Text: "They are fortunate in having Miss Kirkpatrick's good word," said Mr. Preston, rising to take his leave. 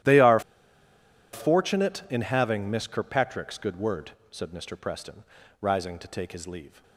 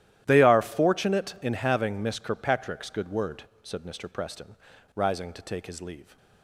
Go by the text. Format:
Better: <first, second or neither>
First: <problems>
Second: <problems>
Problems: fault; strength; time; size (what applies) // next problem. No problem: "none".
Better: second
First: starts louder than the rest; strong; until 1.9 s; 12.5 dB // pauses between "are" and "fortunate"; noticeable; at 0.3 s; 0.93 s long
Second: starts louder than the rest; strong; until 1.2 s; 12.5 dB